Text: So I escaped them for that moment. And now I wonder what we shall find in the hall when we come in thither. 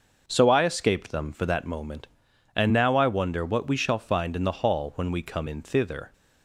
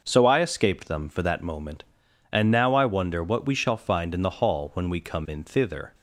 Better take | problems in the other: neither | none

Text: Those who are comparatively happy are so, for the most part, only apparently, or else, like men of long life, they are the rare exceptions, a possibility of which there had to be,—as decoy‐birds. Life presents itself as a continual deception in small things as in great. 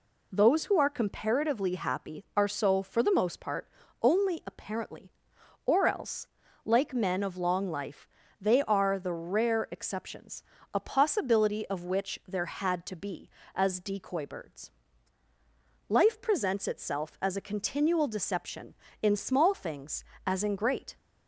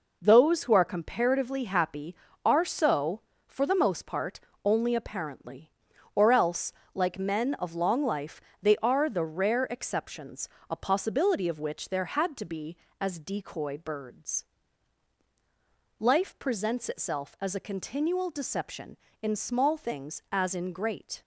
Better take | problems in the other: neither | none

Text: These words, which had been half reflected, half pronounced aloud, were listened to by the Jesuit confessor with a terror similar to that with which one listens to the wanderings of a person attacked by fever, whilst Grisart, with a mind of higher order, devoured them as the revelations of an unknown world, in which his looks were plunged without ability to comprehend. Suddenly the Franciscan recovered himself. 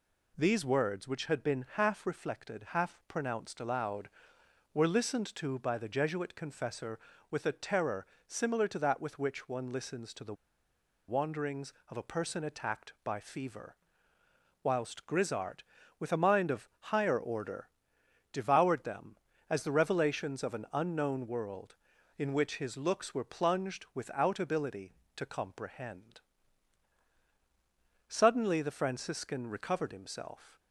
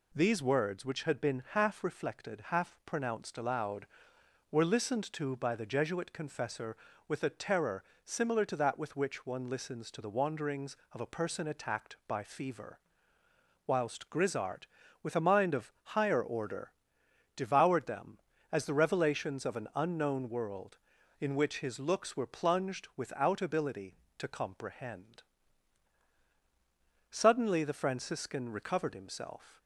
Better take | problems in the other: second | pauses between "terror" and "similar"; slight; at 8.0 s; 0.22 s long; slight in the second // pauses between "the" and "wanderings"; noticeable; at 10.3 s; 0.74 s long

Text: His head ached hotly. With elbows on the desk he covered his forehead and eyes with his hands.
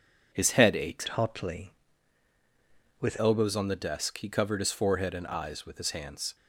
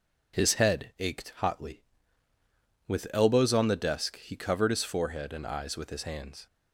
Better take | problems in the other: second | changes voice from "hotly" to "With"; from 1.0 to 3.1 s; 2.1 s long

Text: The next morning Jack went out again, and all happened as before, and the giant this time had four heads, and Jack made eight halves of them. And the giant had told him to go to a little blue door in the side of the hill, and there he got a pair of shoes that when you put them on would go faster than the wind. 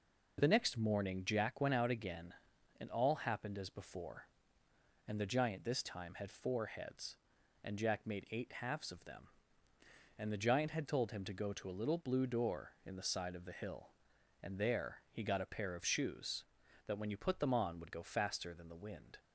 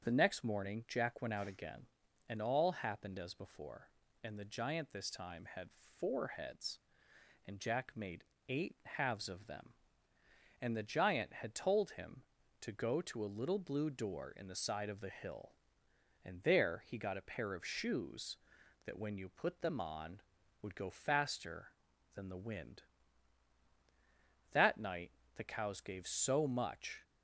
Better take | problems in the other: first | starts louder than the rest; strong; until 1.0 s; 7 dB // pauses between "made" and "eight"; slight; at 8.2 s; 0.24 s long // goes on to say "That night the cows gave so much"; strong; from 24.5 s on; 2.5 s long

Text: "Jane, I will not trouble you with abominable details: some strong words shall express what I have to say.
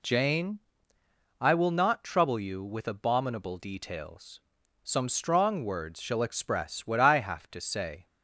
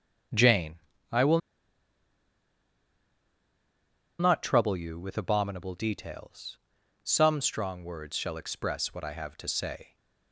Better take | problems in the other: first | starts louder than the rest; strong; until 4.4 s; 7.5 dB // pauses between "will" and "not"; strong; at 1.4 s; 2.8 s long

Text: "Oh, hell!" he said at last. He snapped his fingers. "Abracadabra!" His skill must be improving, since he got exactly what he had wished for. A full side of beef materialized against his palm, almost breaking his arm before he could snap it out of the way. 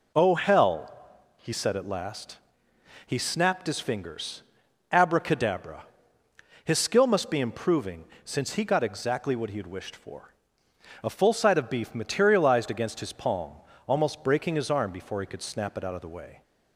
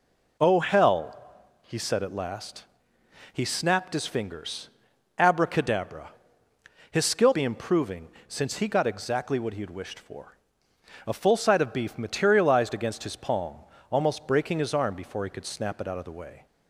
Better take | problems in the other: first | skips "must"; at 7.3 s

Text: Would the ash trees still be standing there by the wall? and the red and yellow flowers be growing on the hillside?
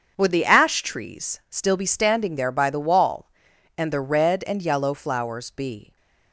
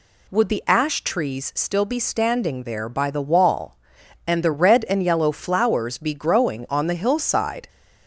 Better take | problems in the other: second | starts louder than the rest; until 1.1 s; 7 dB // stops before "growing on the hillside"; at 5.9 s

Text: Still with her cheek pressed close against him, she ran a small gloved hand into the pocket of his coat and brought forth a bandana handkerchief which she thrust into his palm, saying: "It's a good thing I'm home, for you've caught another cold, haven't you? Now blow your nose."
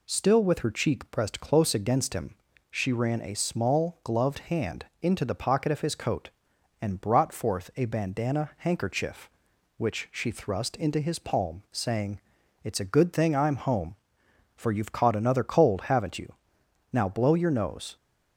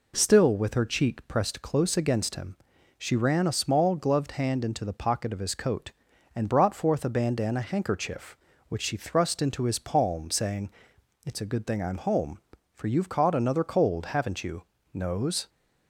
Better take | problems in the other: first | skips "Now blow your"; at 14.7 s

